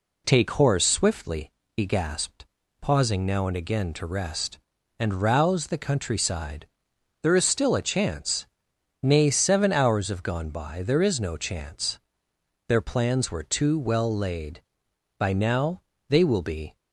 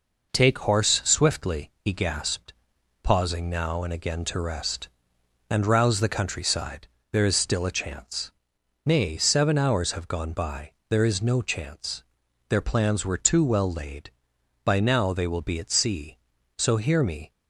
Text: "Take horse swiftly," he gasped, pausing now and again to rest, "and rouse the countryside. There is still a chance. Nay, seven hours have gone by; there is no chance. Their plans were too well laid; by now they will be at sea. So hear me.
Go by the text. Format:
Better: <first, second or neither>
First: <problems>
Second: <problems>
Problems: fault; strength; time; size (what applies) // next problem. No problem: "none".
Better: second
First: pauses between "now" and "they"; slight; at 15.8 s; 0.28 s long // stops before "at sea So hear me"; at 16.7 s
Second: none